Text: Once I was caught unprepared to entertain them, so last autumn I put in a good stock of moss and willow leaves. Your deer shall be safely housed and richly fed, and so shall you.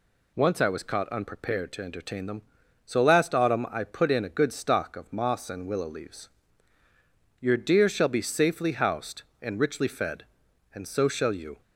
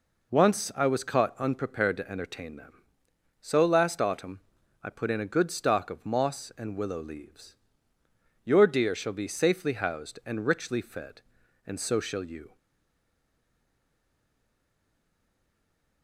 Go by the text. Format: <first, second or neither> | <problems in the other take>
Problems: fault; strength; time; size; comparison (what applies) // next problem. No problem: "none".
first | pauses between "autumn" and "I"; at 4.4 s; 0.42 s long // stays silent after the last word; strong; from 12.5 s on; 3.5 s long